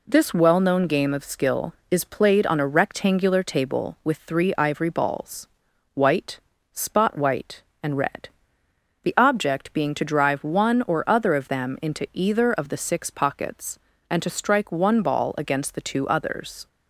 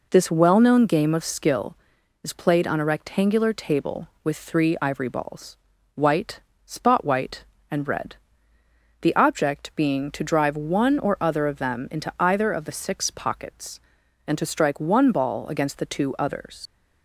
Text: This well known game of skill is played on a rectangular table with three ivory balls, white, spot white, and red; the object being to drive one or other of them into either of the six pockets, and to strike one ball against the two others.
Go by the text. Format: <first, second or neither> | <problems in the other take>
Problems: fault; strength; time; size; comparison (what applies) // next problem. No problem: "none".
first | leaves "others" unfinished; at 16.6 s; 70 ms